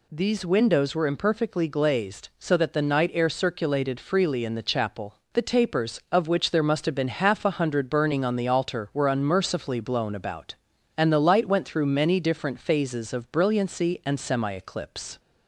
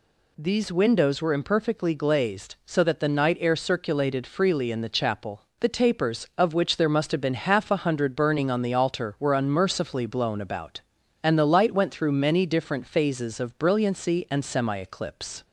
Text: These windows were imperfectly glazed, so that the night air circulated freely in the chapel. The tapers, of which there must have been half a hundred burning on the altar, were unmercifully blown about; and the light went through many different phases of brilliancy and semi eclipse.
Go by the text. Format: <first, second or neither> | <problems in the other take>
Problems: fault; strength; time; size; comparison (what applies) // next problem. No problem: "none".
neither | none